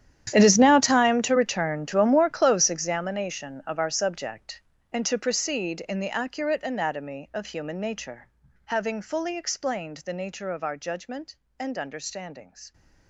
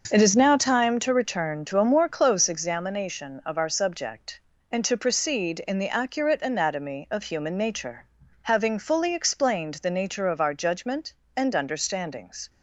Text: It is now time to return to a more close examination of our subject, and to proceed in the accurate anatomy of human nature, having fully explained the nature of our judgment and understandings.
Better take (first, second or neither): second